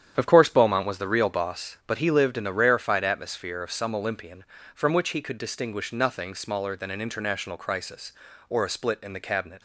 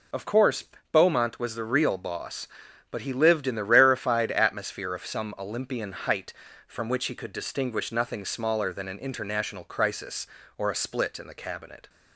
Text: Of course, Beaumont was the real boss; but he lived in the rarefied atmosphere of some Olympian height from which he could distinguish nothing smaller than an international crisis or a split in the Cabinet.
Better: second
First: starts louder than the rest; strong; until 1.1 s; 9.5 dB // skips "height"; at 4.5 s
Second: none

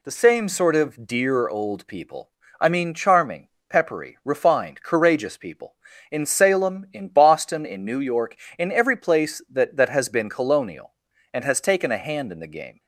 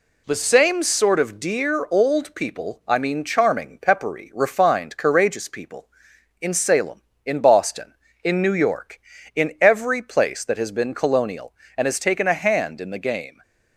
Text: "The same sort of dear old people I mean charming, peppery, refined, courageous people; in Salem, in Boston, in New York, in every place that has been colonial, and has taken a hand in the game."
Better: second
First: pauses between "people" and "I"; slight; at 2.3 s; 0.28 s long // says "that" twice; at 9.7 s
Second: none

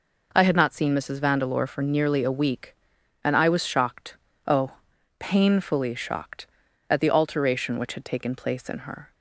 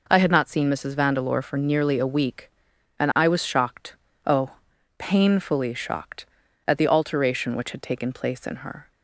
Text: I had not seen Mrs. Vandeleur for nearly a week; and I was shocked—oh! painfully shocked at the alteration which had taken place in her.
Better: neither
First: none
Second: none

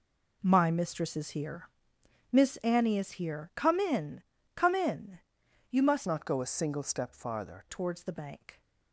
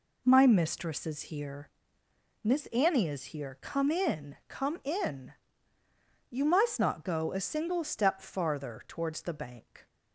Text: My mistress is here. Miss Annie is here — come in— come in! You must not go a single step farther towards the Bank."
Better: second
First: changes voice from "not" to "farther"; from 6.0 to 7.6 s; 1.6 s long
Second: none

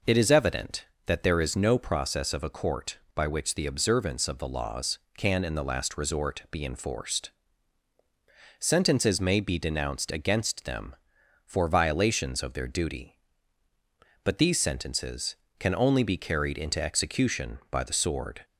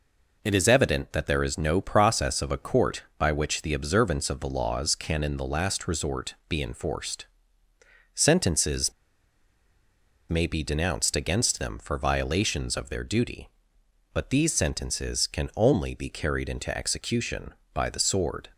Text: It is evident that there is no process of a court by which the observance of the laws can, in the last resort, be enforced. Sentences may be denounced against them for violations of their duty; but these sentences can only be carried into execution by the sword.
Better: first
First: none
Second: pauses between "Sentences" and "may"; strong; at 8.9 s; 1.3 s long

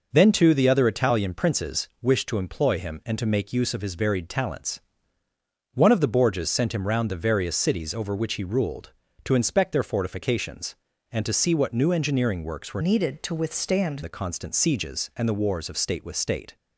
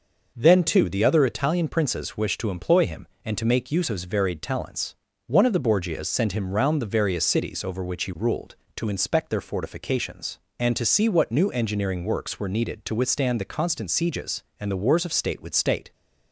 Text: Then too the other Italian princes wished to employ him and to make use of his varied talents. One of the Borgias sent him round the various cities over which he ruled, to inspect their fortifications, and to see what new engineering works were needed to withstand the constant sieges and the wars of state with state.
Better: second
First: changes voice from "needed" to "withstand"; from 12.8 to 14.0 s; 1.2 s long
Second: none

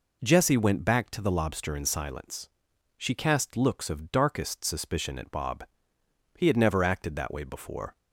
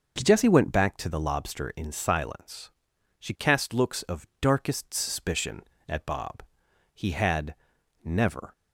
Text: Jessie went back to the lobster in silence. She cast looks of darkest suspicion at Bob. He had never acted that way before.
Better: first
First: none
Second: pauses between "had" and "never"; noticeable; at 7.5 s; 0.50 s long // stops before "acted that way before"; at 8.5 s

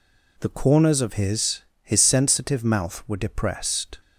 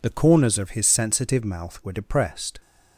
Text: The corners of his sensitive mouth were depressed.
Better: second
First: says "his" twice; at 1.8 s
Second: none

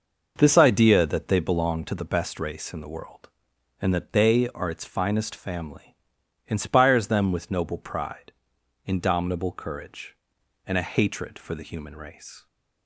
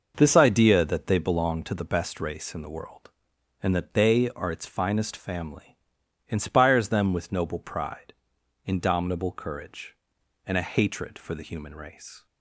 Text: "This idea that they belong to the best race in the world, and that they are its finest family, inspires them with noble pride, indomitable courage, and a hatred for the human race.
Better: neither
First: none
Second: none

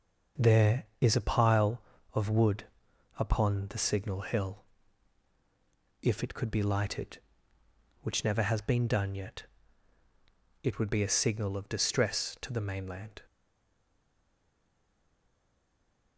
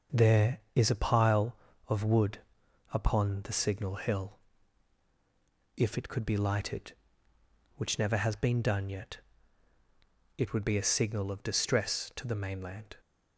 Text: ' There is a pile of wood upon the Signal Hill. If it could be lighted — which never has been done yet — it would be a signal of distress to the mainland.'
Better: second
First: pauses between "wood" and "upon"; noticeable; at 2.6 s; 0.52 s long // stays silent after the last word; strong; from 13.2 s on; 2.9 s long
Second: pauses between "wood" and "upon"; noticeable; at 2.3 s; 0.52 s long

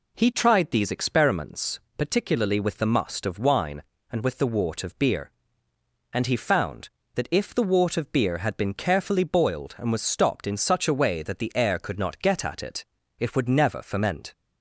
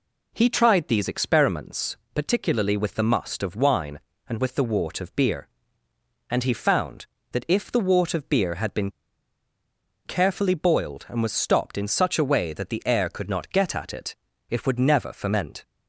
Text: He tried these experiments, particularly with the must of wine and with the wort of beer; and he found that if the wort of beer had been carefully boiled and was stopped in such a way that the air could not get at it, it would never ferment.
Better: first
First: none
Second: pauses between "been" and "carefully"; at 8.8 s; 1.1 s long

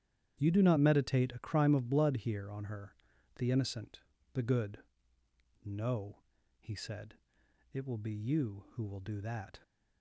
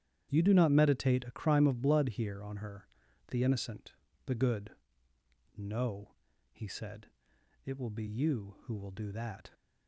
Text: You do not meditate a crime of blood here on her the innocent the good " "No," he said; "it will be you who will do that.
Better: neither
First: starts louder than the rest; strong; until 1.4 s; 10.5 dB // pauses between "her" and "the"; noticeable; at 2.9 s; 0.46 s long // pauses between "innocent" and "the"; slight; at 4.0 s; 0.32 s long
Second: starts louder than the rest; strong; until 1.3 s; 10.5 dB // pauses between "her" and "the"; noticeable; at 2.8 s; 0.46 s long // pauses between "innocent" and "the"; slight; at 3.9 s; 0.32 s long

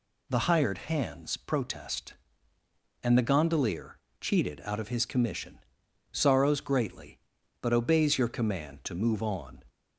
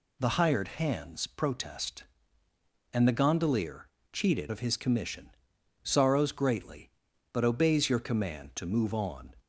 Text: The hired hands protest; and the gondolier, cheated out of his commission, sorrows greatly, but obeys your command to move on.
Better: first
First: none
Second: skips "out"; at 4.4 s

